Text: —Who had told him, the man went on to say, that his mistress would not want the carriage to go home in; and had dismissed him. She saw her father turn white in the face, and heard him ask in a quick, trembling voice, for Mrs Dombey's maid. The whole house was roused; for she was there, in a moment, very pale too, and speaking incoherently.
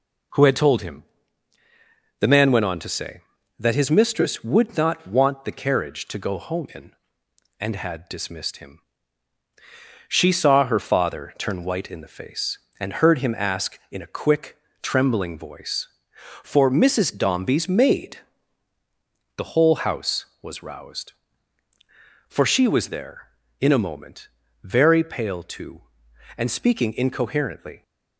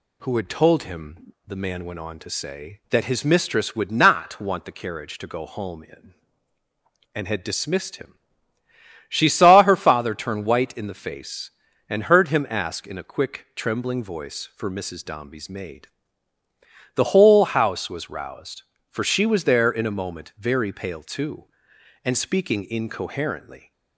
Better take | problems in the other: neither | none

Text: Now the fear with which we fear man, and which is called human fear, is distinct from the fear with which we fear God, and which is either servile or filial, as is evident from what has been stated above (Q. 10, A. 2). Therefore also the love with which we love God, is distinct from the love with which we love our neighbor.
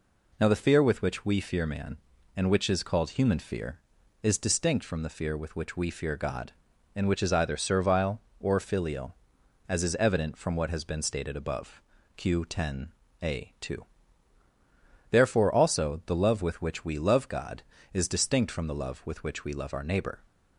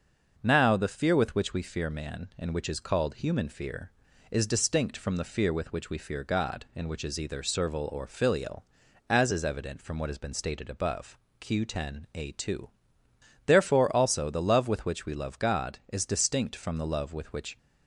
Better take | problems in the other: first | starts louder than the rest; noticeable; until 1.4 s; 6 dB // stops before "we love our neighbor"; at 17.5 s

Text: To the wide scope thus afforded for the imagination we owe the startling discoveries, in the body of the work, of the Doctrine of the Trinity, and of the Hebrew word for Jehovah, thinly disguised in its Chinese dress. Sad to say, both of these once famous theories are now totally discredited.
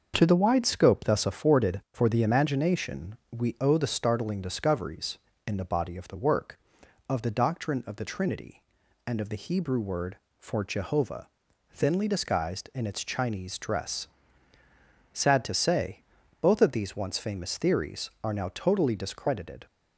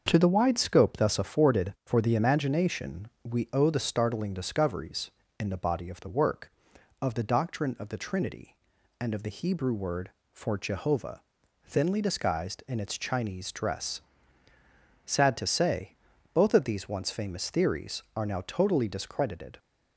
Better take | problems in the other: neither | starts louder than the rest; the same in both // pauses between "imagination" and "we"; slight; the same in both

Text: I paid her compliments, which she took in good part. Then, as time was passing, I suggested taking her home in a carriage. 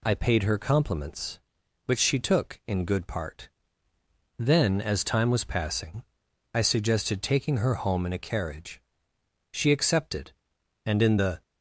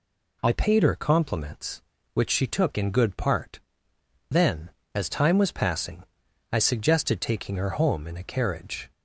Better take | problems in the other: second | goes on to say "She accepted and in the"; strong; from 9.4 s on; 1.9 s long

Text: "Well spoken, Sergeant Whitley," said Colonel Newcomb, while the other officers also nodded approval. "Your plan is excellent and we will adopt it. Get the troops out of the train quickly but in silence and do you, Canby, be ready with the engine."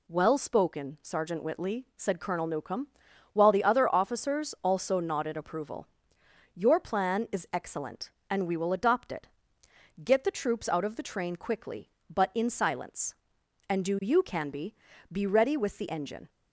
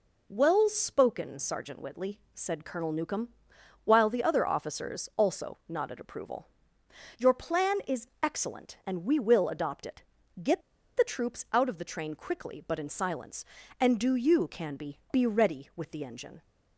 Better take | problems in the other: first | pauses between "is" and "excellent"; slight; at 8.0 s; 0.16 s long // pauses between "Get" and "the"; slight; at 10.6 s; 0.36 s long

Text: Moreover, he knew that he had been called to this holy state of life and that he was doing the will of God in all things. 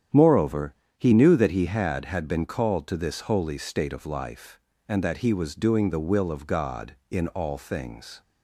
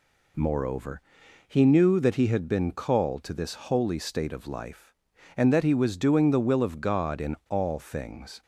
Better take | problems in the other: second | starts louder than the rest; strong; until 1.3 s; 9.5 dB // says "had" twice; at 2.0 s

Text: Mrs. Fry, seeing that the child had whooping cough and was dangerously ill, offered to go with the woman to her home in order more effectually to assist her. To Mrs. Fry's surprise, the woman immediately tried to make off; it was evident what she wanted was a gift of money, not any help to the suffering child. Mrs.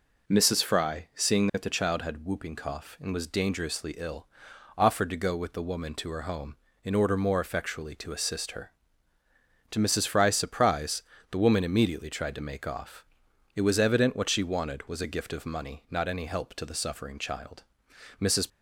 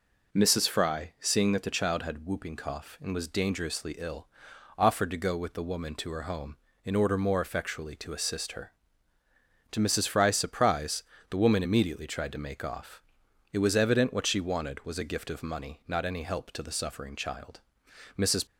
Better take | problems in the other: neither | none

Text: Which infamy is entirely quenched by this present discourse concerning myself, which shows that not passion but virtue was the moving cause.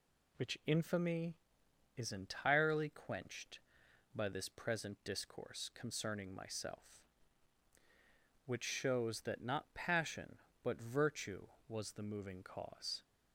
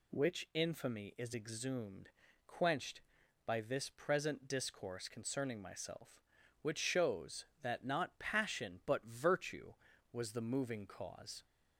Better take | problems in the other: first | says "exhumed" for "entirely"; at 1.3 s

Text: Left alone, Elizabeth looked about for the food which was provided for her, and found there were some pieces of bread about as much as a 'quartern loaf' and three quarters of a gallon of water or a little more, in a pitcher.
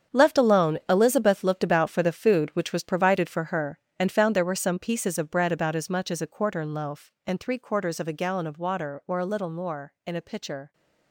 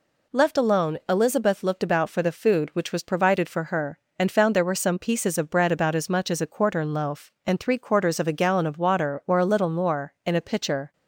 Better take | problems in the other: second | gets quieter; strong; throughout; 12.5 dB

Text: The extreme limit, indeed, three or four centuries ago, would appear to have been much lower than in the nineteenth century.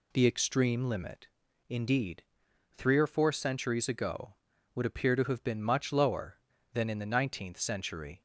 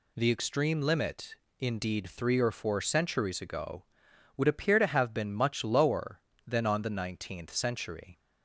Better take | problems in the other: first | says "on" for "in"; at 6.6 s

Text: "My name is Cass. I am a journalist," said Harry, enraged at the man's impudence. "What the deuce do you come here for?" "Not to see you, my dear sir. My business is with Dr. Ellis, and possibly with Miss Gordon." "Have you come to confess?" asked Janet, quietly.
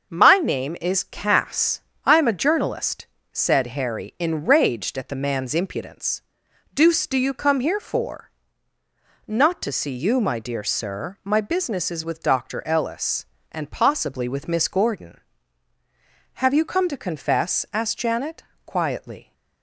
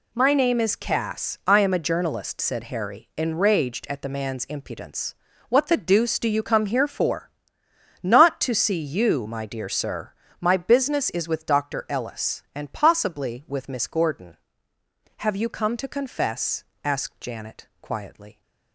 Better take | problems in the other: second | starts louder than the rest; until 1.1 s; 6.5 dB // skips "What the"; at 6.4 s

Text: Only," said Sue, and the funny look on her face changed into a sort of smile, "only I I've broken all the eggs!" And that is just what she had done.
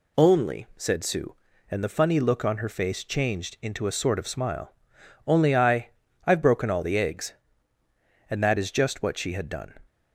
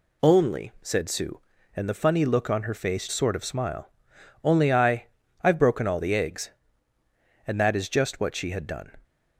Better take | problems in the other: first | skips "changed into a"; at 3.0 s // pauses between "I" and "I've"; at 5.0 s; 0.38 s long; also in the first

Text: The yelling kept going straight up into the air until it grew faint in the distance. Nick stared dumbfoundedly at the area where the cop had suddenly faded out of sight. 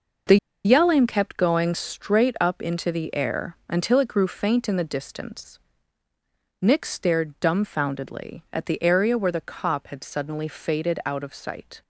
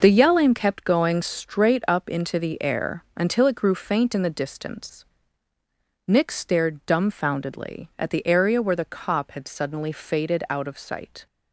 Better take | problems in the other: second | pauses between "The" and "yelling"; slight; at 0.3 s; 0.28 s long

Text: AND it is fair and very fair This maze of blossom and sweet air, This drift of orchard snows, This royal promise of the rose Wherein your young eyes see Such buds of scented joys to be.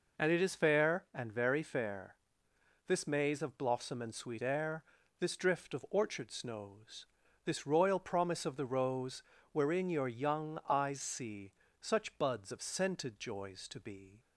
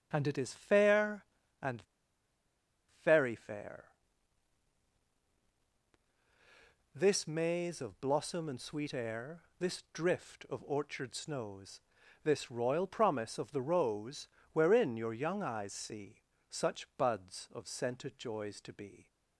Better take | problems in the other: first | starts louder than the rest; until 1.1 s; 7 dB // pauses between "and" and "very"; at 1.8 s; 1.2 s long // pauses between "fair" and "This"; strong; at 3.8 s; 3.1 s long; noticeable in the first // pauses between "rose" and "Wherein"; slight; at 14.2 s; 0.26 s long; slight in the first // pauses between "see" and "Such"; slight; at 16.1 s; 0.34 s long; slight in the first

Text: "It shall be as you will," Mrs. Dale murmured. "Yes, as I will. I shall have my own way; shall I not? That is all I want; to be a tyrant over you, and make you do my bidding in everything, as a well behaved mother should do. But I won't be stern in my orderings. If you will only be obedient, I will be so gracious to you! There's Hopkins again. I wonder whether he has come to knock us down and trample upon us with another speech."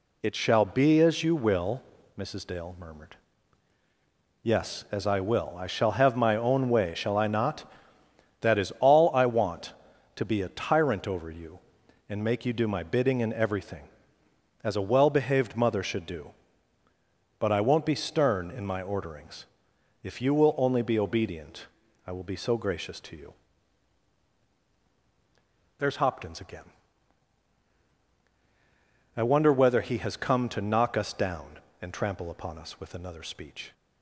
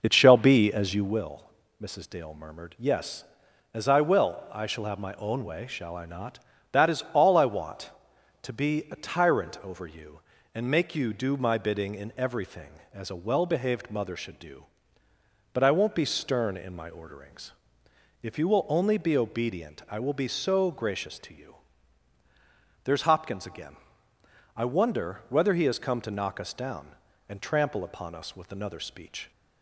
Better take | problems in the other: first | starts louder than the rest; noticeable; until 1.3 s; 5.5 dB

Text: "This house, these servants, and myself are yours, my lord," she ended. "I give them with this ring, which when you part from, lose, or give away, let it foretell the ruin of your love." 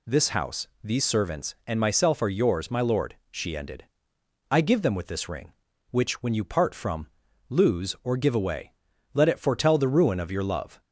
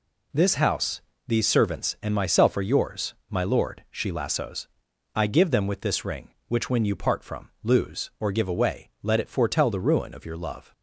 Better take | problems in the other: first | says "lassos" for "ended"; at 4.1 s

